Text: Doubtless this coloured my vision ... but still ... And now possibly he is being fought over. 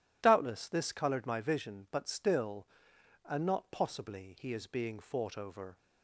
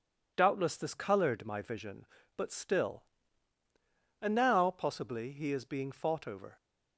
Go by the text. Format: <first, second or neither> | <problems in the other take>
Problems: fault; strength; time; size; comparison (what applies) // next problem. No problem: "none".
second | says "not" for "now"; at 3.4 s